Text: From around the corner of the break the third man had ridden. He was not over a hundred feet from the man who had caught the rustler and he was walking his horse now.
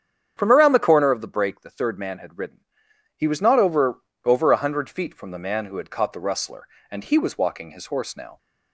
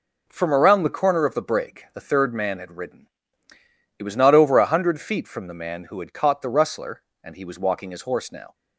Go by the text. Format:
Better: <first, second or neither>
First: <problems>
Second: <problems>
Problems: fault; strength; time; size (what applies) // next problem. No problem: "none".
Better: second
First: starts louder than the rest; strong; until 1.3 s; 8.5 dB // says "over" twice; at 4.2 s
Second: none